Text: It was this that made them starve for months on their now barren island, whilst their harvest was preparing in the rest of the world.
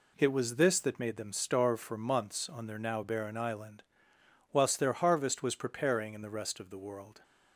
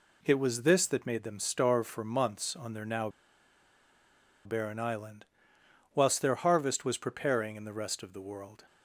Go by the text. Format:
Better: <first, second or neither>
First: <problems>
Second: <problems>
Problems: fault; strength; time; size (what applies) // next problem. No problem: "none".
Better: first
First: none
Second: pauses between "now" and "barren"; strong; at 3.0 s; 1.3 s long